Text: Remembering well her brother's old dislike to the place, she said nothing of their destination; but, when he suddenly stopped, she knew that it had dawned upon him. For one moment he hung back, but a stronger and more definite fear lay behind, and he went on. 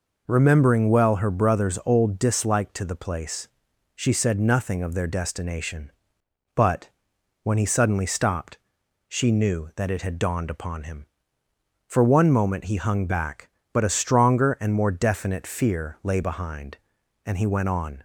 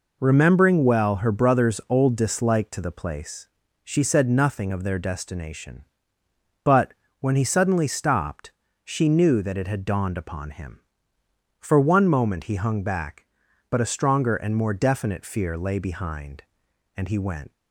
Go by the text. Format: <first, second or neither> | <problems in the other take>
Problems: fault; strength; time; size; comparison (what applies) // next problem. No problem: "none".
first | stops before "on"; at 17.5 s